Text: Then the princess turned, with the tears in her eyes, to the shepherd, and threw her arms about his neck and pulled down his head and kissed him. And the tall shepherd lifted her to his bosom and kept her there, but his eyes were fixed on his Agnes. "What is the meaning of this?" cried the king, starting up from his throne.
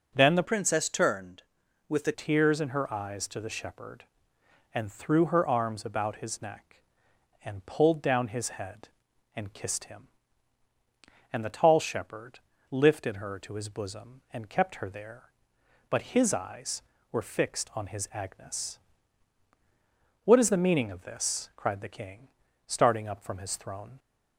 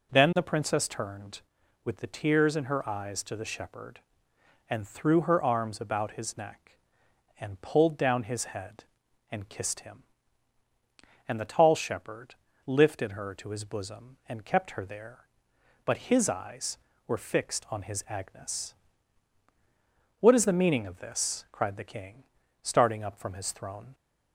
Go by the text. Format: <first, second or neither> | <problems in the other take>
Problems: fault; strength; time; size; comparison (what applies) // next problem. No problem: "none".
second | changes voice from "princess" to "the"; from 0.4 to 2.1 s; 1.7 s long // pauses between "shepherd" and "lifted"; slight; at 12.3 s; 0.32 s long; slight in the second